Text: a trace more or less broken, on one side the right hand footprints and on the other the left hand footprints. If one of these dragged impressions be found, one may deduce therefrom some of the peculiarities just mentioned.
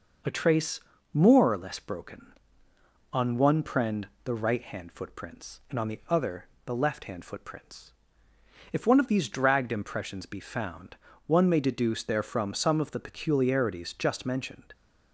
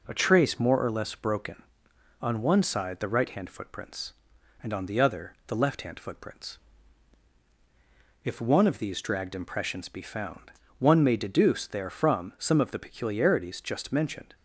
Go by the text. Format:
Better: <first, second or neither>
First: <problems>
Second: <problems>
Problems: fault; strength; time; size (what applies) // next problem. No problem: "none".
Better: second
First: pauses between "trace" and "more"; slight; at 0.8 s; 0.32 s long // says "prend" for "side"; at 3.6 s // pauses between "other" and "the"; slight; at 6.4 s; 0.18 s long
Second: none